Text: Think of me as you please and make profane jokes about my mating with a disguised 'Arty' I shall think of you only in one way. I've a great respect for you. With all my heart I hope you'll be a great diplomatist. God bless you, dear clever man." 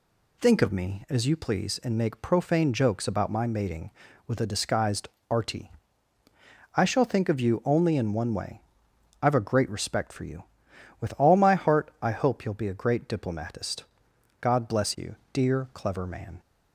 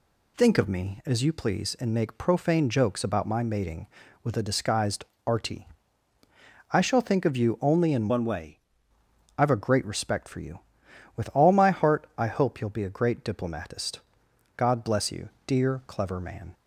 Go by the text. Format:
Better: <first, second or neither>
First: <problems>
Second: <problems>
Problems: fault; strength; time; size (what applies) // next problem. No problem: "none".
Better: first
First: pauses between "disguised" and "Arty"; slight; at 5.0 s; 0.22 s long // pauses between "Arty" and "I"; at 5.7 s; 1.0 s long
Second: pauses between "disguised" and "Arty"; slight; at 5.0 s; 0.22 s long // pauses between "Arty" and "I"; at 5.6 s; 1.0 s long // changes voice from "one" to "way"; from 8.0 to 8.5 s; 0.5 s long